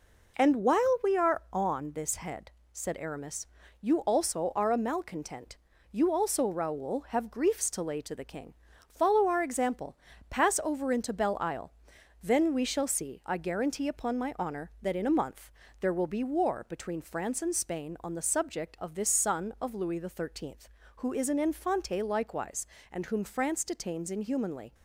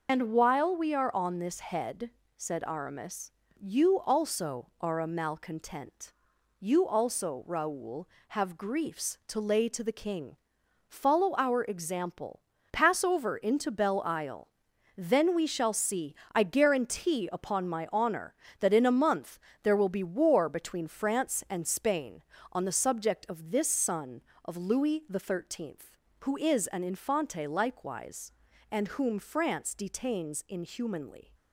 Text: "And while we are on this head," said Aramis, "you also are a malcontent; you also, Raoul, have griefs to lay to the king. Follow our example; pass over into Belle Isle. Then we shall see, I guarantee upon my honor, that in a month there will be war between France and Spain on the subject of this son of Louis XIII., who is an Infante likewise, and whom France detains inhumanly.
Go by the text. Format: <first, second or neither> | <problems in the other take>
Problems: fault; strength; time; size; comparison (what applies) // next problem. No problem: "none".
first | loses the start of "And"; at 0.0 s; 65 ms // pauses between "month" and "there"; slight; at 19.3 s; 0.24 s long; slight in the first